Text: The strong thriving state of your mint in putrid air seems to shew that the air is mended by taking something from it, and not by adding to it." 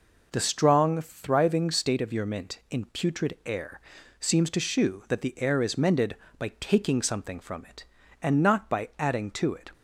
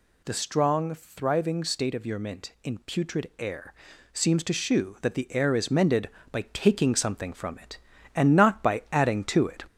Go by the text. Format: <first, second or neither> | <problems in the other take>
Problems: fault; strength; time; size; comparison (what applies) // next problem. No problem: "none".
first | gets louder; slight; throughout; 3.5 dB // pauses between "air" and "seems"; at 3.7 s; 0.40 s long; also in the first